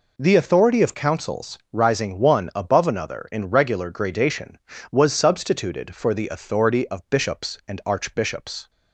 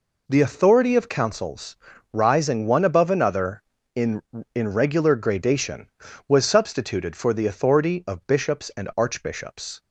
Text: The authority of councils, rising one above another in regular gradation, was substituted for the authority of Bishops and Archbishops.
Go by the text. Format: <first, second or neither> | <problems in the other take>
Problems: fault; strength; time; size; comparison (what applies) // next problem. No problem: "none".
first | says "in" twice; at 4.5 s